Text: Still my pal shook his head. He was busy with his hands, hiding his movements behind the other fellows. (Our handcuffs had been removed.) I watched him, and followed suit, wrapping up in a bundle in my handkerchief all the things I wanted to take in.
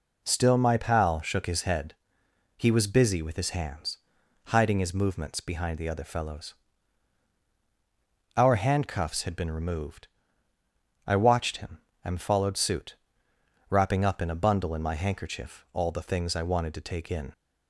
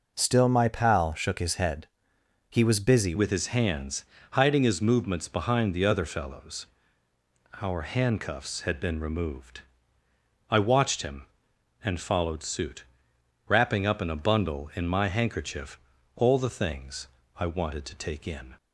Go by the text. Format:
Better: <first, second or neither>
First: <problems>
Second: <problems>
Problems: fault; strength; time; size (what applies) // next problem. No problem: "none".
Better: first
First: none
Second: changes voice at "with"; from 3.1 s on; 15.4 s long // pauses between "handkerchief" and "all"; slight; at 15.7 s; 0.36 s long // pauses between "things" and "I"; slight; at 17.0 s; 0.30 s long